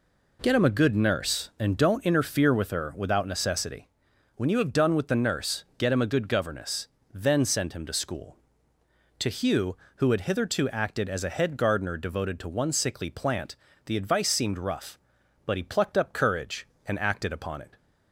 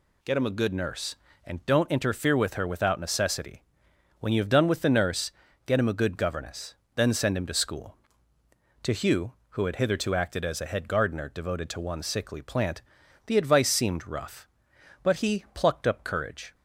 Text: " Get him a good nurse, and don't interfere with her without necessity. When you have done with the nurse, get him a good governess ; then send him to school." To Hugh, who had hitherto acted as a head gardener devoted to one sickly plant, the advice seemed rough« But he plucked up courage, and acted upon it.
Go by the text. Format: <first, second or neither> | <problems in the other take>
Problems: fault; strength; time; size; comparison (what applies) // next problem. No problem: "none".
first | stops before "and acted upon it"; at 16.5 s